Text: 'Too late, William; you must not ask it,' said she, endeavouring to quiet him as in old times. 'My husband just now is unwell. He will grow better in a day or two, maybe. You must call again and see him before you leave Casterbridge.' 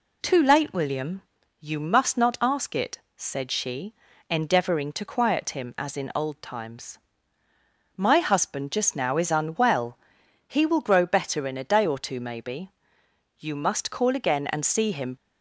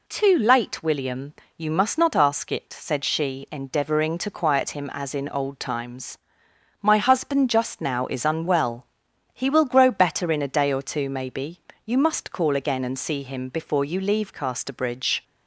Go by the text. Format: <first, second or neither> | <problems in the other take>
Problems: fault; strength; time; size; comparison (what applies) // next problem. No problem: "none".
second | stops before "before you leave Casterbridge"; at 15.1 s